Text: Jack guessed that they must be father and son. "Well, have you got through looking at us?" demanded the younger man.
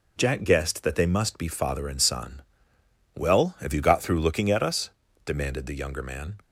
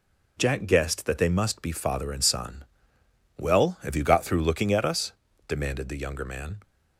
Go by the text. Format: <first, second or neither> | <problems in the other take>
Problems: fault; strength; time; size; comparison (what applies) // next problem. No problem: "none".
neither | none